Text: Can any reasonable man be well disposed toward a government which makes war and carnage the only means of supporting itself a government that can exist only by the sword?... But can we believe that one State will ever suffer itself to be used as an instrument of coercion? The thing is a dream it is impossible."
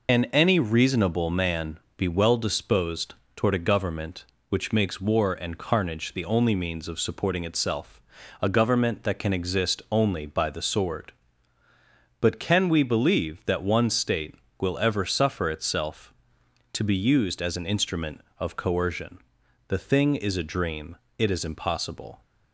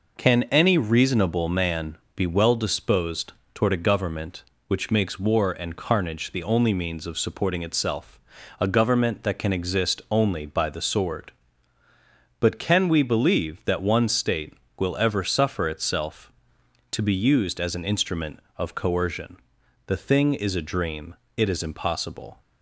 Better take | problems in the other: second | loses the start of "Can"; at 0.0 s; 115 ms // pauses between "man" and "be"; slight; at 1.7 s; 0.16 s long; slight in the second // pauses between "disposed" and "toward"; slight; at 3.1 s; 0.20 s long; slight in the second // pauses between "itself" and "a"; at 7.9 s; 0.40 s long; also in the second // pauses between "dream" and "it"; slight; at 20.9 s; 0.20 s long; slight in the second

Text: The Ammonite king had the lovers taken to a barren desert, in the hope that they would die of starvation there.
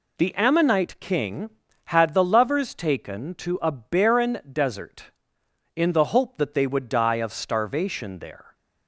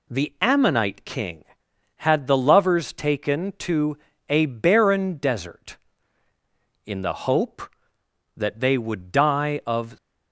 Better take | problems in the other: first | pauses between "to" and "a"; slight; at 3.9 s; 0.28 s long // stops before "starvation there"; at 9.9 s

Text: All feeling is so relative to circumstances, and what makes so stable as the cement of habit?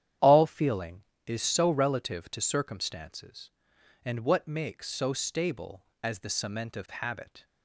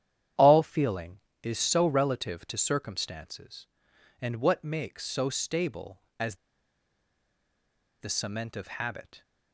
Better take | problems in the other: first | starts louder than the rest; strong; until 1.6 s; 10 dB; strong in the first // pauses between "as" and "the"; strong; at 6.3 s; 1.6 s long

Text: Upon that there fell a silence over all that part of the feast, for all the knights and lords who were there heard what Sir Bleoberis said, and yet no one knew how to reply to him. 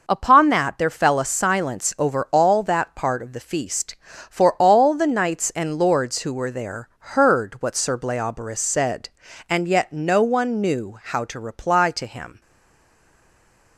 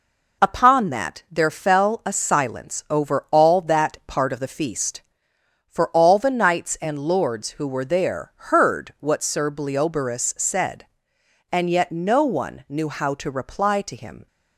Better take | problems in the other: second | stays silent after the last word; noticeable; from 12.4 s on; 1.3 s long

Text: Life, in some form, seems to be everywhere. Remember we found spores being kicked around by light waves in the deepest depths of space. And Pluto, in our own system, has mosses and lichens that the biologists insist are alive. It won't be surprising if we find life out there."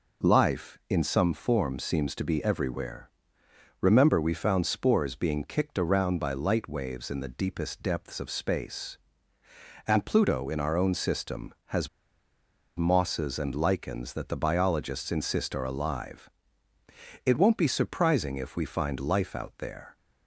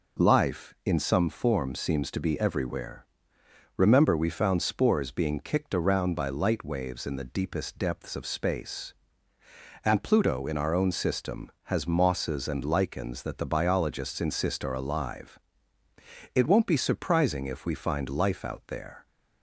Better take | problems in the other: second | pauses between "has" and "mosses"; noticeable; at 11.8 s; 0.89 s long

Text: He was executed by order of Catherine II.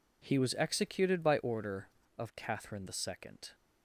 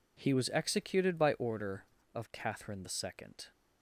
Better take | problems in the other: neither | none

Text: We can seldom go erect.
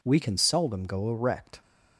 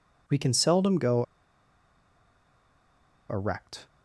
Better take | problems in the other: first | pauses between "go" and "erect"; strong; at 1.2 s; 2.0 s long

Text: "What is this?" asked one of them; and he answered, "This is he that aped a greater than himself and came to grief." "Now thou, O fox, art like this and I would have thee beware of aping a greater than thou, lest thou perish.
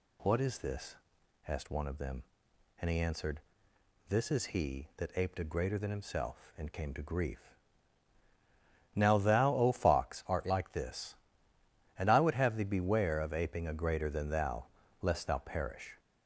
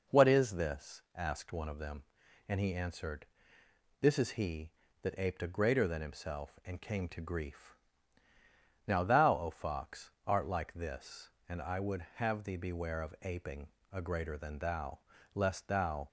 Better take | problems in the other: first | pauses between "aping" and "a"; slight; at 13.6 s; 0.24 s long // stops before "perish"; at 16.0 s

